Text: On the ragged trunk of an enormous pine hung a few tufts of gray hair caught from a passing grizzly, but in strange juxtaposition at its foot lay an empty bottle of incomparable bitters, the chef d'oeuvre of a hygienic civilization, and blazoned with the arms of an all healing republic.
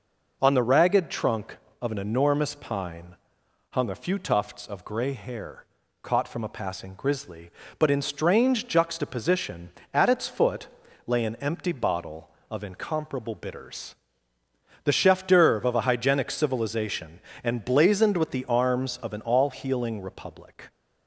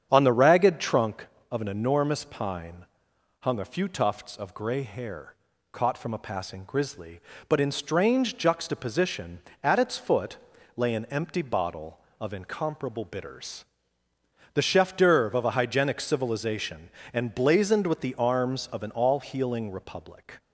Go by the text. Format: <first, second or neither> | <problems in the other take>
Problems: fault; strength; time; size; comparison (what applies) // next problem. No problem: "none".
first | starts louder than the rest; strong; until 1.2 s; 8 dB // pauses between "pine" and "hung"; noticeable; at 2.8 s; 0.56 s long; noticeable in the first // pauses between "hair" and "caught"; slight; at 5.3 s; 0.36 s long; slight in the first // pauses between "foot" and "lay"; at 10.3 s; 0.38 s long; also in the first